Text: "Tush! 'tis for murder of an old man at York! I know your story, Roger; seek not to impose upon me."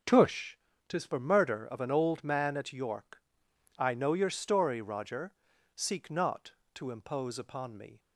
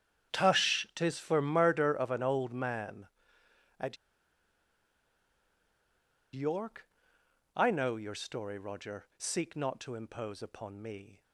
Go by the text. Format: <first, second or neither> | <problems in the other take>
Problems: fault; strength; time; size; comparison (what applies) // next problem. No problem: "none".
first | starts louder than the rest; strong; until 1.4 s; 9 dB // pauses between "at" and "York"; strong; at 3.9 s; 2.3 s long